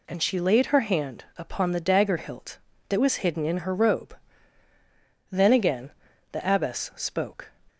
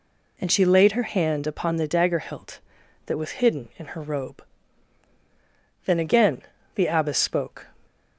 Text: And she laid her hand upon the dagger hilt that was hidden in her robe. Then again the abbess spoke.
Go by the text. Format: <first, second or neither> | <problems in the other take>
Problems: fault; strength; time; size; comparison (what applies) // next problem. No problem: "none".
neither | pauses between "again" and "the"; the same in both